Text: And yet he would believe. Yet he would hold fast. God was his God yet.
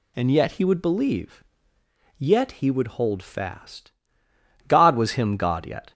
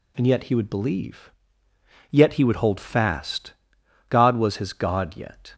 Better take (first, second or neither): second